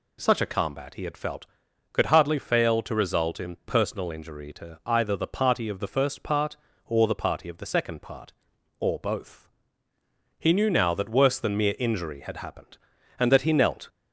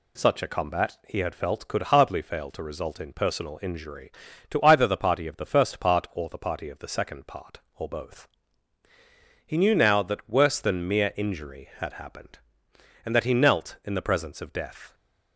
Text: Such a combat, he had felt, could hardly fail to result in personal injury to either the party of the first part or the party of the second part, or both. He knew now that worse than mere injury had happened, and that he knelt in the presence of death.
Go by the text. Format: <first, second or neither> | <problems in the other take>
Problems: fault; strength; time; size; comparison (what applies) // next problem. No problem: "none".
second | stops before "in the presence of death"; at 13.8 s